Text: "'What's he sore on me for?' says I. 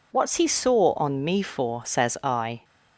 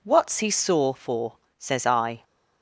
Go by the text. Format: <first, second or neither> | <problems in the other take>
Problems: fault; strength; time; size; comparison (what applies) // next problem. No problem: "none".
first | skips "on me"; at 0.9 s